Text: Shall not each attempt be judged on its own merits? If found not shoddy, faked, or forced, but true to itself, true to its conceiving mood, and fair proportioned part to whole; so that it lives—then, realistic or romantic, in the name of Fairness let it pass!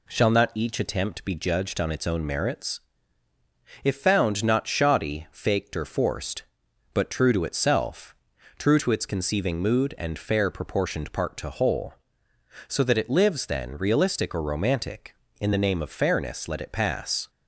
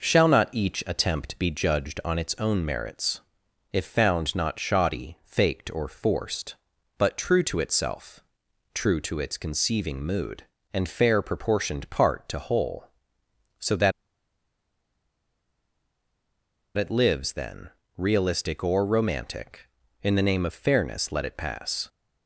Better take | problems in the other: first | pauses between "that" and "it"; strong; at 13.9 s; 2.8 s long

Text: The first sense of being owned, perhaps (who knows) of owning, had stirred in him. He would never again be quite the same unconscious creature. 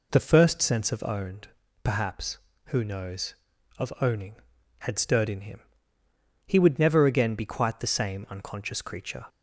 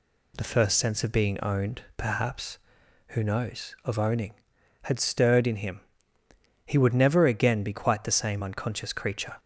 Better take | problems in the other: second | skips "being"; at 1.0 s

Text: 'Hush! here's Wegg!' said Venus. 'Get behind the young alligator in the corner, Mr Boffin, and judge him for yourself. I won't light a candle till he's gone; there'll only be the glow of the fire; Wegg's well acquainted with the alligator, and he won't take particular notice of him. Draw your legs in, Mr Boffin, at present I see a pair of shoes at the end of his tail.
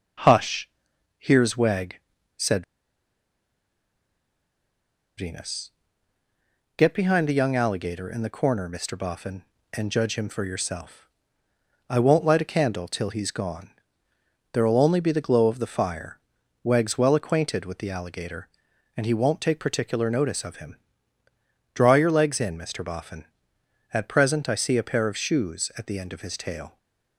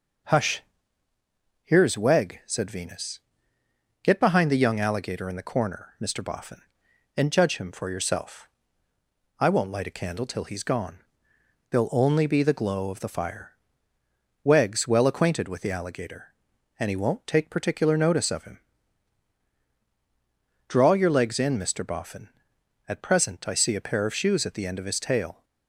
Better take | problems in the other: second | starts louder than the rest; until 1.7 s; 7 dB // pauses between "said" and "Venus"; strong; at 2.6 s; 2.5 s long

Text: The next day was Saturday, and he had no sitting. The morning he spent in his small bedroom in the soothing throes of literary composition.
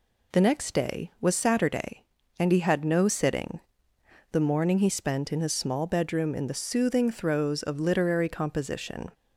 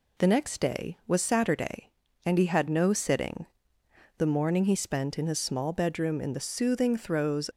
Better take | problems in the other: first | stops before "of literary composition"; at 7.5 s

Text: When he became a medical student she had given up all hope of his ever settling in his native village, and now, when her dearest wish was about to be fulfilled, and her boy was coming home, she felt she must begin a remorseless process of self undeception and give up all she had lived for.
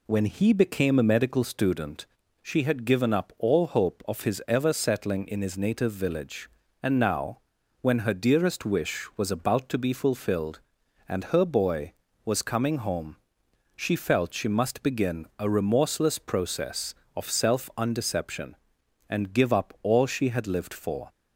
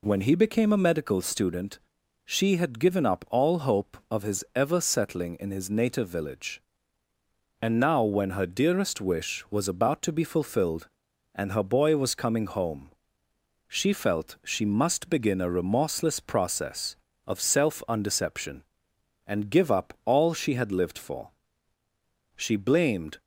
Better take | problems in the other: first | pauses between "student" and "she"; noticeable; at 1.7 s; 0.48 s long; slight in the first // goes on to say "She blamed"; noticeable; from 22.3 s on; 0.84 s long

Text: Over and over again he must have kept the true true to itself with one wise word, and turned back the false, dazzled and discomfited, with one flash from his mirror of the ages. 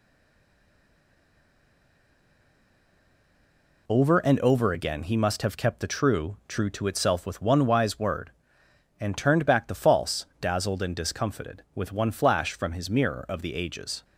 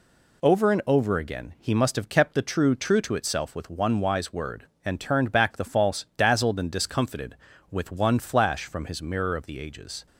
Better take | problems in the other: second | stays silent before the first word; strong; until 3.8 s; 3.8 s long

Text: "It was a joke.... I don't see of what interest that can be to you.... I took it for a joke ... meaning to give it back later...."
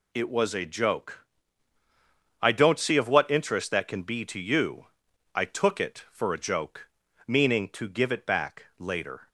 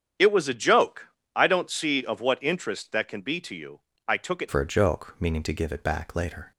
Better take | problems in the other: first | starts louder than the rest; strong; until 1.4 s; 8.5 dB // changes voice at "for"; from 4.4 s on; 2.1 s long

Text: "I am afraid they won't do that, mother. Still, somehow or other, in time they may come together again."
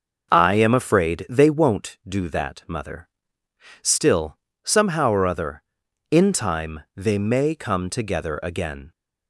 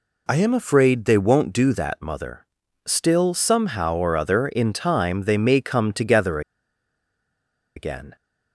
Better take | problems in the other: first | pauses between "together" and "again"; strong; at 6.4 s; 1.3 s long

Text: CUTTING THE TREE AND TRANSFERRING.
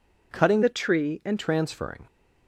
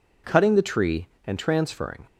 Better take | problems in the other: second | changes voice from "THE" to "AND"; from 0.6 to 1.3 s; 0.7 s long

